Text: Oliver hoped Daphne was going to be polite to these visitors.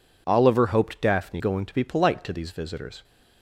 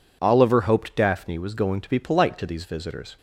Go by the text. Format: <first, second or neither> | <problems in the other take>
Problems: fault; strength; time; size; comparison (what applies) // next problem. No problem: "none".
second | skips "was"; at 1.3 s